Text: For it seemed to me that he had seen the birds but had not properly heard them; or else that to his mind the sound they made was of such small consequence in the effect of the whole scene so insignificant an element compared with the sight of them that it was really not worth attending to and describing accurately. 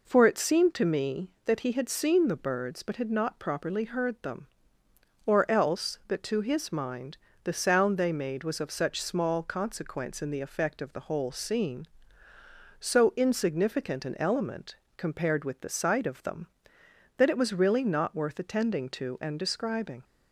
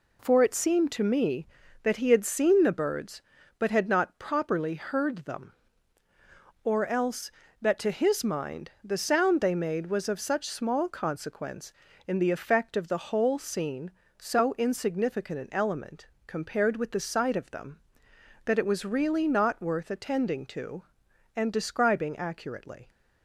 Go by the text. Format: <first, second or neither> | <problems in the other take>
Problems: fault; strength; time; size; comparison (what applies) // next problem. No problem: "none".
second | pauses between "mind" and "the"; slight; at 7.1 s; 0.26 s long // pauses between "element" and "compared"; slight; at 14.7 s; 0.22 s long; slight in the second // stops before "accurately"; at 20.0 s